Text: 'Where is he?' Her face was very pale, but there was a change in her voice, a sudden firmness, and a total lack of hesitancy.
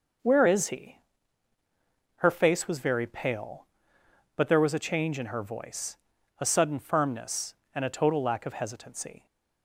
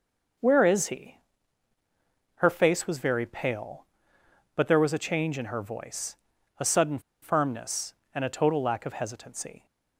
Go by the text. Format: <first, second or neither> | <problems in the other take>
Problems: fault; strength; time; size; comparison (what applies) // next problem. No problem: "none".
first | pauses between "sudden" and "firmness"; slight; at 6.9 s; 0.22 s long